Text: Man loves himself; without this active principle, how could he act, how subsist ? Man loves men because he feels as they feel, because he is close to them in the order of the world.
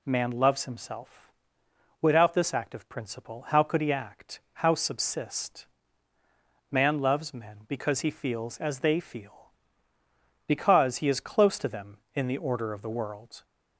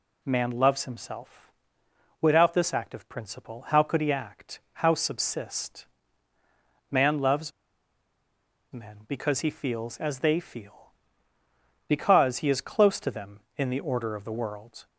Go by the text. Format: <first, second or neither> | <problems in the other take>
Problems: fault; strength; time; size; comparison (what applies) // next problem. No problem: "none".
first | pauses between "loves" and "men"; at 7.5 s; 1.2 s long